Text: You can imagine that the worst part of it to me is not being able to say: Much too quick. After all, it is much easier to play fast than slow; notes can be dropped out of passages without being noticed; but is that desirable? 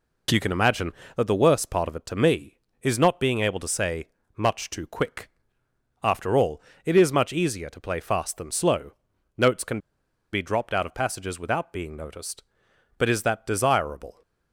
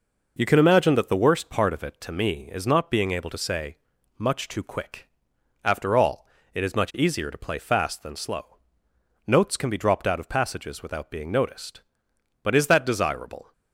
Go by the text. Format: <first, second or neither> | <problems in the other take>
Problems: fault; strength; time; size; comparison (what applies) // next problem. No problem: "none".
second | pauses between "can" and "be"; noticeable; at 9.7 s; 0.53 s long